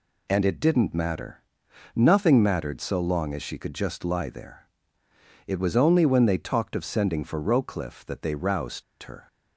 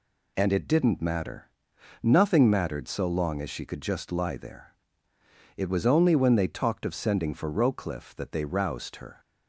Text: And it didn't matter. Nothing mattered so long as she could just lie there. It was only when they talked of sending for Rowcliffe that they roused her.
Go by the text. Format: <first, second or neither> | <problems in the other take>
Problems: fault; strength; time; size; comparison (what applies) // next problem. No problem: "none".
second | pauses between "roused" and "her"; slight; at 8.8 s; 0.20 s long